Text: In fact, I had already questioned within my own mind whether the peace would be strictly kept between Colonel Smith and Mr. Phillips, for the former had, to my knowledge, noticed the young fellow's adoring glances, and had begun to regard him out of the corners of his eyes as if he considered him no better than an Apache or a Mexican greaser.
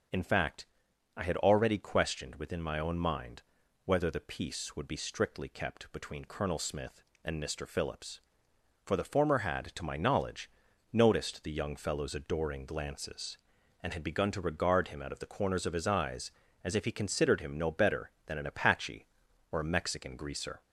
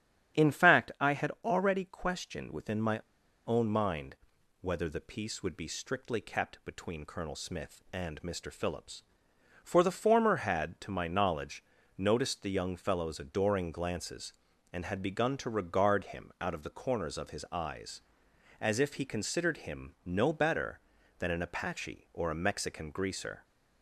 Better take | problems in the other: first | starts louder than the rest; strong; until 1.5 s; 9.5 dB; also in the first // pauses between "my" and "own"; noticeable; at 2.9 s; 0.48 s long // pauses between "mind" and "whether"; noticeable; at 4.1 s; 0.46 s long; also in the first

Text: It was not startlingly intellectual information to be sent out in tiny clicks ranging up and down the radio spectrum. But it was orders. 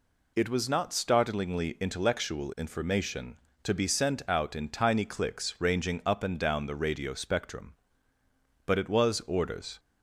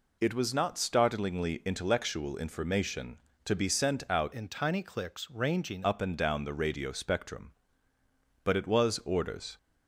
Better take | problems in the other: first | changes voice from "in" to "ranging"; from 4.3 to 5.8 s; 1.5 s long

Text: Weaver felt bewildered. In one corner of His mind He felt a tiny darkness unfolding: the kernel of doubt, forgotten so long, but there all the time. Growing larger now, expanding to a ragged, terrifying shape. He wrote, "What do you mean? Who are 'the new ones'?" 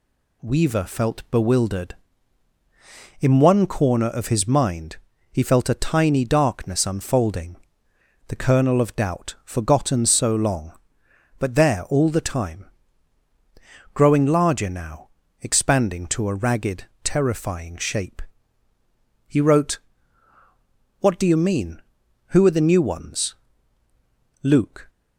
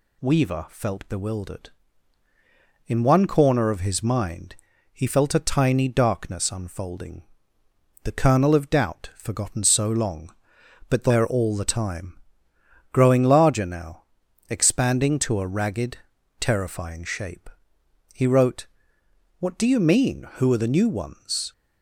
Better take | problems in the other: second | pauses between "mind" and "He"; slight; at 4.9 s; 0.34 s long; slight in the second // goes on to say "Luke"; slight; from 24.4 s on; 0.46 s long

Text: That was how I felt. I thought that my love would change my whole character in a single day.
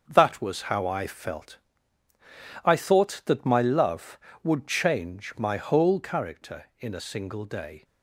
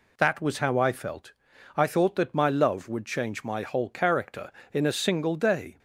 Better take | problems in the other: second | gets quieter; throughout; 6 dB

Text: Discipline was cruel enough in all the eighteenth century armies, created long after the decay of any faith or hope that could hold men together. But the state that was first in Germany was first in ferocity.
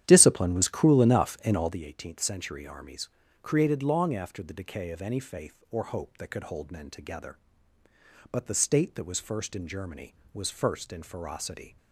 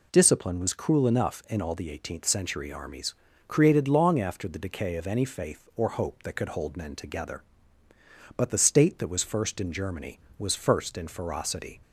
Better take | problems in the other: second | starts louder than the rest; strong; until 1.9 s; 10.5 dB

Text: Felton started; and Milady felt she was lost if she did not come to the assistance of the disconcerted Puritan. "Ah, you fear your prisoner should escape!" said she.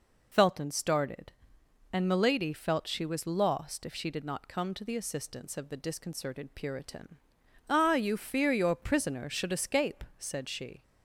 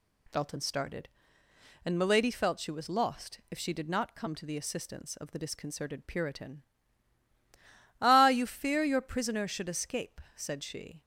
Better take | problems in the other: second | loses the start of "Felton"; at 0.3 s; 25 ms

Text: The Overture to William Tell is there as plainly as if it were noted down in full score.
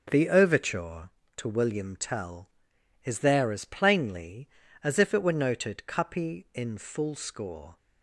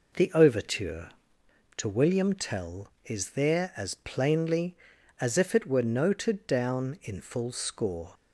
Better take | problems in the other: second | starts louder than the rest; until 1.1 s; 6 dB // says "cuppy" for "down"; at 5.8 s

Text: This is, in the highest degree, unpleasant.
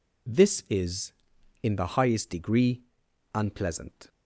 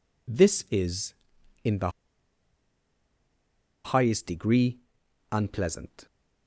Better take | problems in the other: first | pauses between "the" and "highest"; strong; at 1.8 s; 1.9 s long

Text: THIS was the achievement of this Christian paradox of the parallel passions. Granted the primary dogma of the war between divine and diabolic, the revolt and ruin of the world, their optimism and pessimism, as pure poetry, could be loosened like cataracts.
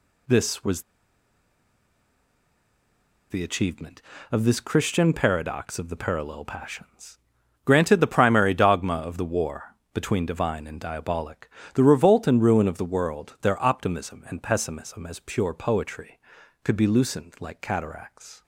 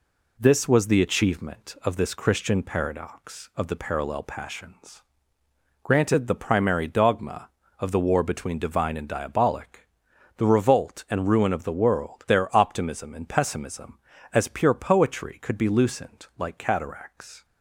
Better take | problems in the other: second | pauses between "was" and "the"; strong; at 0.8 s; 2.4 s long // pauses between "war" and "between"; slight; at 9.7 s; 0.18 s long

